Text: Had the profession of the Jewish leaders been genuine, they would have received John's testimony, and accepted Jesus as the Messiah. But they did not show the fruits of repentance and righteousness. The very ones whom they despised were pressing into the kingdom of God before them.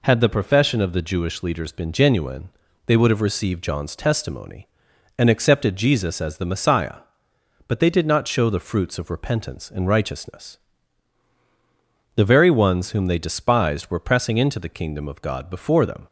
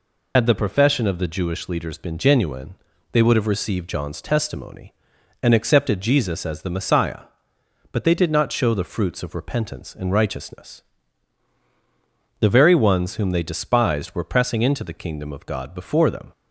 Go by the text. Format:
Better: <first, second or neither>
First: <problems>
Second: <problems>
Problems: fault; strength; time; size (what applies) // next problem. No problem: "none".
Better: first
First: none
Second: loses the start of "Had"; at 0.3 s; 60 ms